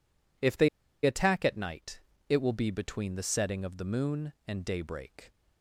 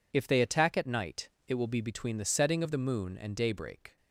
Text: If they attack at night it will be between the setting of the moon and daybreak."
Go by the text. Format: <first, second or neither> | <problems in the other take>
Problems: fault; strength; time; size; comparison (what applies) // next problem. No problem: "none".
second | pauses between "they" and "attack"; slight; at 0.6 s; 0.35 s long // pauses between "night" and "it"; slight; at 1.9 s; 0.30 s long; slight in the second